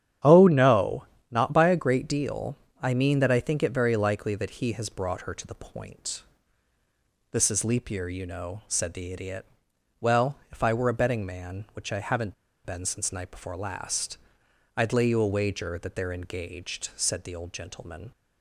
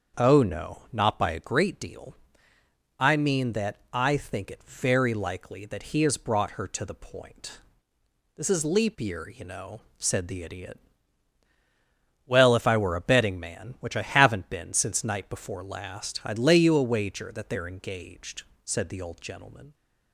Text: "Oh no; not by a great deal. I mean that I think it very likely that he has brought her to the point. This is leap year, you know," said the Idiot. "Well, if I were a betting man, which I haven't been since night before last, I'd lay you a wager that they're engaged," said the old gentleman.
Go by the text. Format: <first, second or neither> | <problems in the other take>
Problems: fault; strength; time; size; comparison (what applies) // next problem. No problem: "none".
second | starts louder than the rest; strong; until 1.4 s; 9.5 dB; also in the second // pauses between "haven't" and "been"; slight; at 12.3 s; 0.32 s long